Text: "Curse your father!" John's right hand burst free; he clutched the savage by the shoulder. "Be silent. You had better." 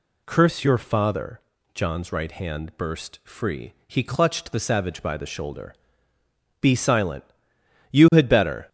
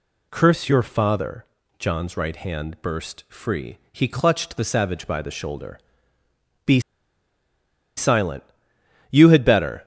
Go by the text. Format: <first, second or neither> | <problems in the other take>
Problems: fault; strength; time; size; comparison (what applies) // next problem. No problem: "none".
first | pauses between "Be" and "silent"; at 6.7 s; 1.1 s long